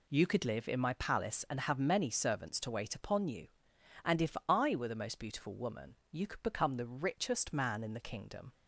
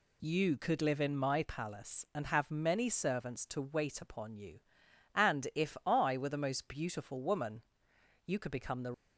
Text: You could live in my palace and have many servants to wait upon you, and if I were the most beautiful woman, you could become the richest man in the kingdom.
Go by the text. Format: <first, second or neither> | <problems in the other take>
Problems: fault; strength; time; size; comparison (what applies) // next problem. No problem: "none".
first | stops before "richest man in the kingdom"; at 8.9 s